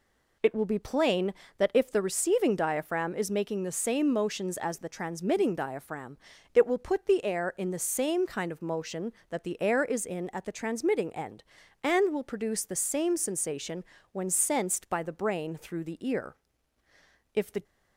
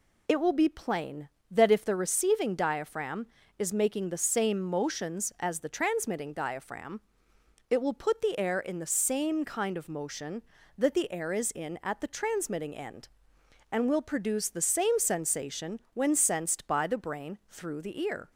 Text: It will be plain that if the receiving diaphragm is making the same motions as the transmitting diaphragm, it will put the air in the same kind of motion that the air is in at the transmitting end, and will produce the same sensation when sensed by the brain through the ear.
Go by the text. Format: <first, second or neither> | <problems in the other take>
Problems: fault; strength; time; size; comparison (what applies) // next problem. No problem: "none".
second | pauses between "sensation" and "when"; slight; at 13.8 s; 0.28 s long // goes on to say "If the"; slight; from 17.3 s on; 0.30 s long